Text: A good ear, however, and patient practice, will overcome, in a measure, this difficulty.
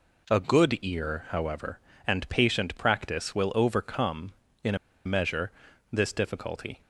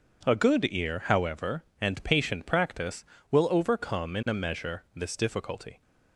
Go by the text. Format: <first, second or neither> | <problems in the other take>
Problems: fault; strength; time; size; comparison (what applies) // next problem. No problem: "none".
second | pauses between "a" and "measure"; slight; at 4.7 s; 0.29 s long